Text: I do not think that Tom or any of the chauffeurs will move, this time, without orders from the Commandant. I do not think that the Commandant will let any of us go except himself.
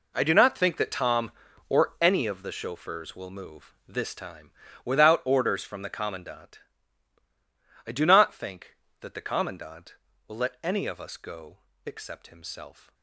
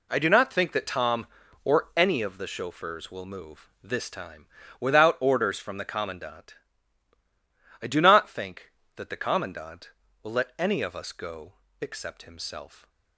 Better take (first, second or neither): second